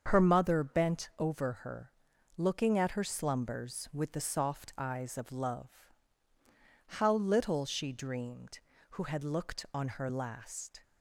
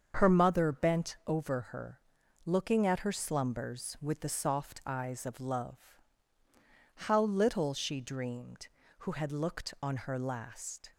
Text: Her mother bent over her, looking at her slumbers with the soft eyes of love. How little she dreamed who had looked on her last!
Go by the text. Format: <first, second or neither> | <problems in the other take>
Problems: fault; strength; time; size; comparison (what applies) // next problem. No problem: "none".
neither | starts louder than the rest; the same in both